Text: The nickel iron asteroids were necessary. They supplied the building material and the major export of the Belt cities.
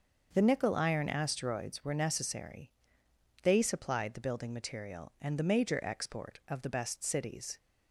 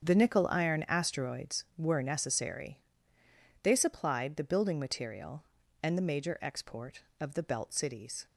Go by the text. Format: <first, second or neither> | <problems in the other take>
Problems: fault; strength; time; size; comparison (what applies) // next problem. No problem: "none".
second | starts louder than the rest; until 1.3 s; 6.5 dB; strong in the second // says "Best" for "Belt"; at 6.6 s